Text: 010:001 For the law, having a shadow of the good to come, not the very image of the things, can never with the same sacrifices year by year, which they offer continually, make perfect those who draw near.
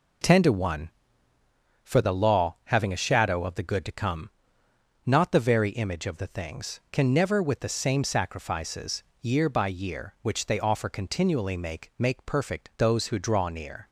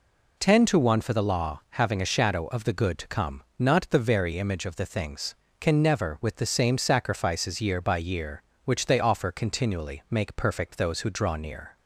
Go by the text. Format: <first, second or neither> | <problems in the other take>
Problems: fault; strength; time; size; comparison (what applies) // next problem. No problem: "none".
second | pauses between "sacrifices" and "year"; slight; at 9.0 s; 0.18 s long // says "make" twice; at 11.9 s